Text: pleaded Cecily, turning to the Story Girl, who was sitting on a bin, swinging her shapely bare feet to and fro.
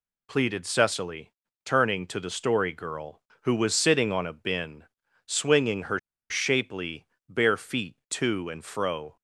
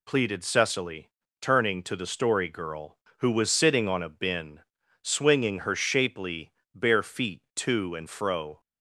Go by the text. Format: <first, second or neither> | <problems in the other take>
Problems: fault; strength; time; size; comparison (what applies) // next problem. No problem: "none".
second | pauses between "her" and "shapely"; slight; at 5.9 s; 0.30 s long // pauses between "shapely" and "bare"; slight; at 7.0 s; 0.22 s long; slight in the second